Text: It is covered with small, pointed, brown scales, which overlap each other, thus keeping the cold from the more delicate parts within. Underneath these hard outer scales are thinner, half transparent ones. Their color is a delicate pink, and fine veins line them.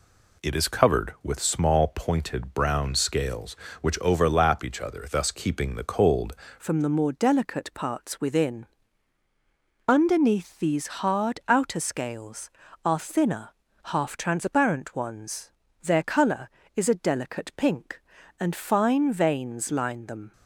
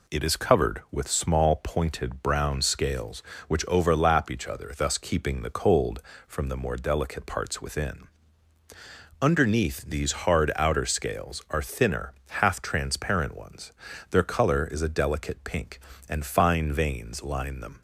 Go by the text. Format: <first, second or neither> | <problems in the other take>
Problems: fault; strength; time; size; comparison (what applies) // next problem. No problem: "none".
second | changes voice at "from"; from 6.5 s on; 13.8 s long